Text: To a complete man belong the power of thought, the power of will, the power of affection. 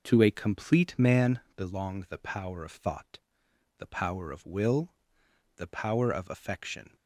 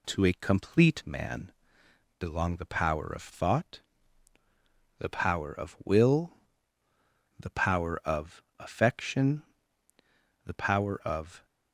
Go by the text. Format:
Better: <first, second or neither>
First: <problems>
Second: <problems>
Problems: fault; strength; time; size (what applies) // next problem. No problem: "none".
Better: first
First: pauses between "man" and "belong"; slight; at 1.4 s; 0.16 s long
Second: pauses between "man" and "belong"; noticeable; at 1.5 s; 0.66 s long // goes on to say "The power of"; noticeable; from 10.4 s on; 1.0 s long